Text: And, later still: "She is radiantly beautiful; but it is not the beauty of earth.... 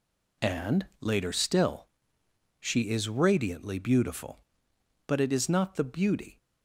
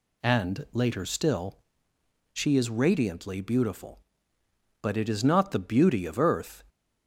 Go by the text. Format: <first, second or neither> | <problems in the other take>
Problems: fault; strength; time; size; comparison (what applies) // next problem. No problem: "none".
second | stops before "of earth"; at 6.3 s